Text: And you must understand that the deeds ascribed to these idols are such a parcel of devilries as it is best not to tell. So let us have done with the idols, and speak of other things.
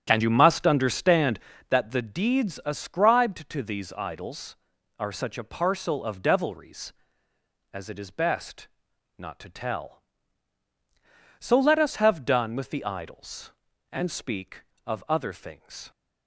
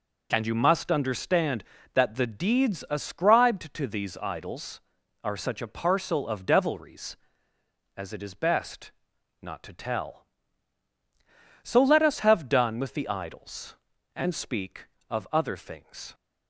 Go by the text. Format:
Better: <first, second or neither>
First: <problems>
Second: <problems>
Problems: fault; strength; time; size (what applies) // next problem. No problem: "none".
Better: second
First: starts louder than the rest; strong; until 1.7 s; 9 dB // pauses between "best" and "not"; noticeable; at 8.6 s; 0.50 s long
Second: pauses between "best" and "not"; noticeable; at 8.9 s; 0.50 s long